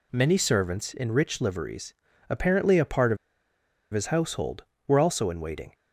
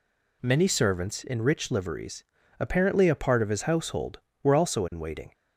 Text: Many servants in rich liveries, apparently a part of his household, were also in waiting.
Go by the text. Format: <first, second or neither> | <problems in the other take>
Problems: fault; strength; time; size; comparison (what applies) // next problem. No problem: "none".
second | pauses between "of" and "his"; noticeable; at 3.1 s; 0.76 s long